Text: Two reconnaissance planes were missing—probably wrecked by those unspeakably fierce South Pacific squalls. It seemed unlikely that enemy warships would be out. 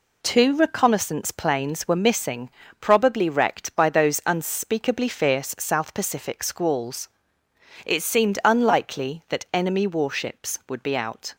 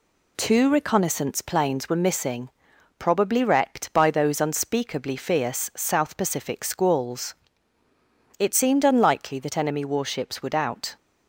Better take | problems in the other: first | skips "be"; at 10.5 s

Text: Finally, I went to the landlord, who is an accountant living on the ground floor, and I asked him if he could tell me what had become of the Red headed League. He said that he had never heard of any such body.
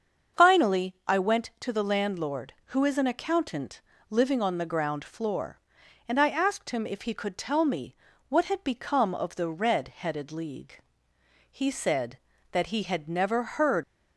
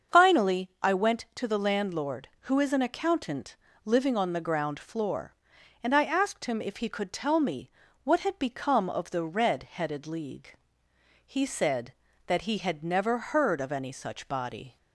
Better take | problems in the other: second | starts louder than the rest; until 1.4 s; 7 dB; also in the second // pauses between "accountant" and "living"; slight; at 3.7 s; 0.30 s long; slight in the second // pauses between "me" and "what"; slight; at 7.9 s; 0.36 s long; slight in the second // stops before "of any such body"; at 13.8 s

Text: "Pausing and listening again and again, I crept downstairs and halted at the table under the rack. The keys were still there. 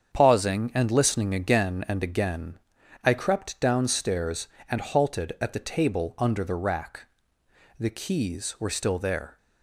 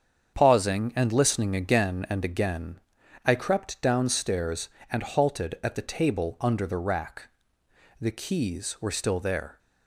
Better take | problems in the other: neither | starts louder than the rest; strong; the same in both

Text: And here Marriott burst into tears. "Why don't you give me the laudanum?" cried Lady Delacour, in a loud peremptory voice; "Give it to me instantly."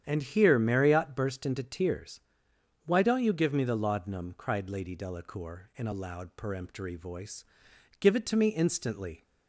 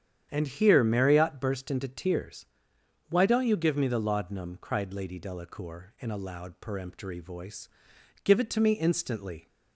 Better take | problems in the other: neither | starts louder than the rest; strong; the same in both

